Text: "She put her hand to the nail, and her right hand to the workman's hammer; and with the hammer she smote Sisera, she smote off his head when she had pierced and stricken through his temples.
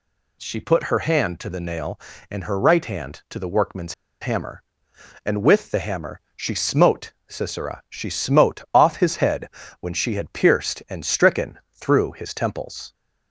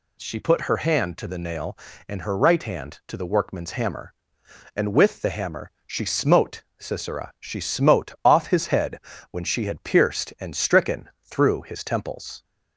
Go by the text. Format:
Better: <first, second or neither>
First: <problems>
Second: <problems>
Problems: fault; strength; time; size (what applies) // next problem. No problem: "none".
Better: second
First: pauses between "workman's" and "hammer"; slight; at 3.9 s; 0.27 s long // pauses between "head" and "when"; slight; at 9.4 s; 0.32 s long // pauses between "stricken" and "through"; slight; at 11.5 s; 0.16 s long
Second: pauses between "head" and "when"; slight; at 8.9 s; 0.32 s long // pauses between "stricken" and "through"; slight; at 11.0 s; 0.15 s long